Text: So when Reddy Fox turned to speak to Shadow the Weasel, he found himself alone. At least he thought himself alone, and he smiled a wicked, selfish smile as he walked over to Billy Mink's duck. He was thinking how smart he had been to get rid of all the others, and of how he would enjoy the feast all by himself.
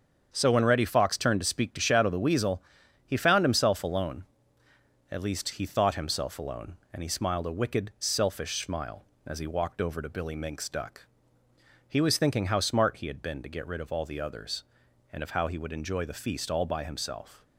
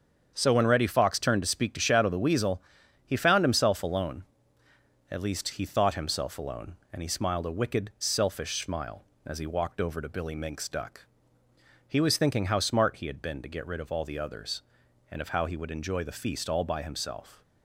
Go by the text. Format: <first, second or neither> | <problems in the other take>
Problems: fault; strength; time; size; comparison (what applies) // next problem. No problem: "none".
neither | starts louder than the rest; strong; the same in both